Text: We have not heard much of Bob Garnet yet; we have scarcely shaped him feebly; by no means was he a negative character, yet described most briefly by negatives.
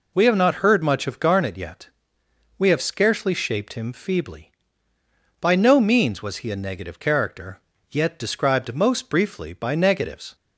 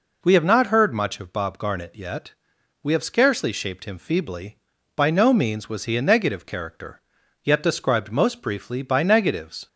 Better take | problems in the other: second | skips "Bob"; at 1.1 s

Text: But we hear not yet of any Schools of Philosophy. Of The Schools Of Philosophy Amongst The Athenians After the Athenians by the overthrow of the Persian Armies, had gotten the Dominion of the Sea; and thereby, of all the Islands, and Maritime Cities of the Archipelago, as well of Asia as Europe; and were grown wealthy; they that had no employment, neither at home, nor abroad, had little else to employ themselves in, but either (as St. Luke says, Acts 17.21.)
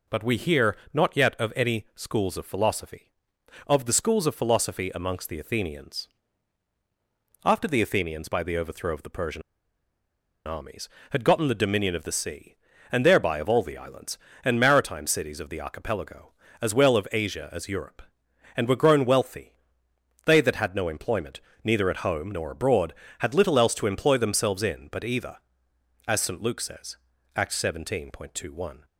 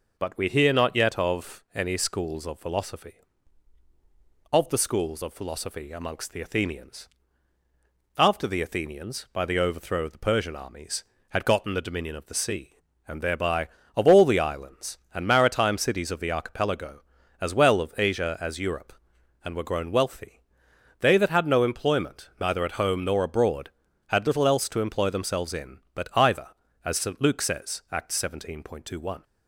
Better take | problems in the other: second | pauses between "hear" and "not"; slight; at 0.7 s; 0.18 s long // pauses between "Athenians" and "After"; strong; at 6.0 s; 1.3 s long; also in the second // pauses between "Persian" and "Armies"; at 9.4 s; 1.0 s long

